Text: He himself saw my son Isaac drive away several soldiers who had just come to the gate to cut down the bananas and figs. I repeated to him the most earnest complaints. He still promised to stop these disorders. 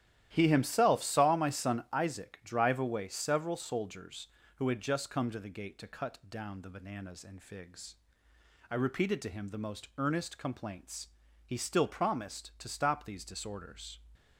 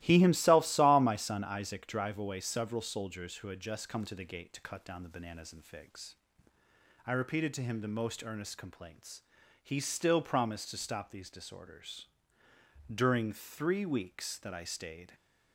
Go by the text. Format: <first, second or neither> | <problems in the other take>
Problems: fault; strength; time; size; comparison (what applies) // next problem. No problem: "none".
first | starts louder than the rest; strong; until 1.0 s; 16.5 dB; strong in the first // goes on to say "During three weeks that I stayed"; strong; from 12.9 s on; 2.2 s long